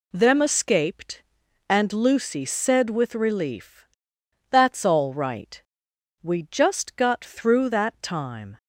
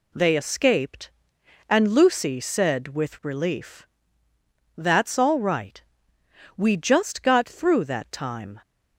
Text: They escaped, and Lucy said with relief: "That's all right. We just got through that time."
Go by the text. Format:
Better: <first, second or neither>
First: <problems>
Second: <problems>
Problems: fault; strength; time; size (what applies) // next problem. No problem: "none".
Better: second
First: says "Them" for "They"; at 0.1 s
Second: none